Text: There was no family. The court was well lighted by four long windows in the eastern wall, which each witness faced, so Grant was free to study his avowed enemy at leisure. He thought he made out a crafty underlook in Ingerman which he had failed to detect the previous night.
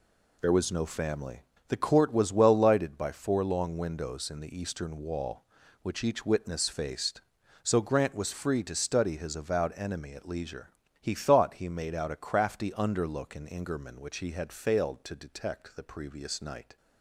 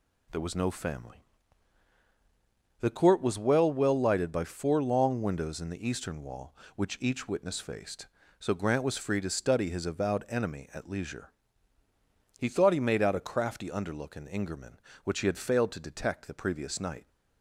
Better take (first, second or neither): first